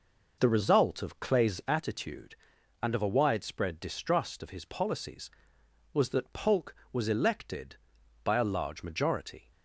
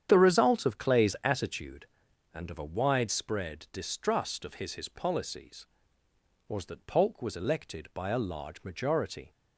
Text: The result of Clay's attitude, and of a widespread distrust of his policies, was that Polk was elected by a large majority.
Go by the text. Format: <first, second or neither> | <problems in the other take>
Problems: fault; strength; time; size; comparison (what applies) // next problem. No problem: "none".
first | starts louder than the rest; strong; until 1.1 s; 9 dB // says "his" twice; at 4.7 s